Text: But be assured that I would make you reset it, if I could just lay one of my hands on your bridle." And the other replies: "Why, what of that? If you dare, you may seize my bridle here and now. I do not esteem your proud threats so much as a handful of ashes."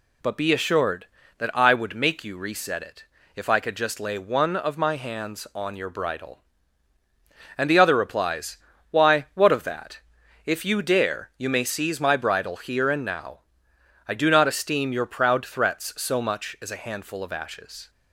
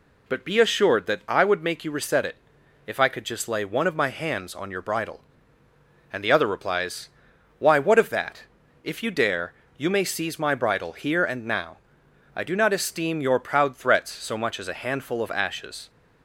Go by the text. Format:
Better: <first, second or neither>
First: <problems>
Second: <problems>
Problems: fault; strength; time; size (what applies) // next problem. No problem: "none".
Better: neither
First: none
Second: none